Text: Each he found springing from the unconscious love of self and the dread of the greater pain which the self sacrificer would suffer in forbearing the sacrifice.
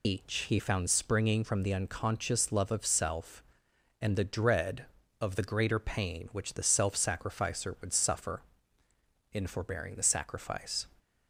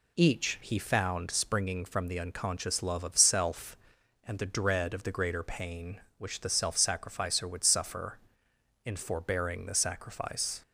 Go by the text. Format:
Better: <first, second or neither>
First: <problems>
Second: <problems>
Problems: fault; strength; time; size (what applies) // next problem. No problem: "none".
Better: second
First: loses the start of "Each"; at 0.0 s; 120 ms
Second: none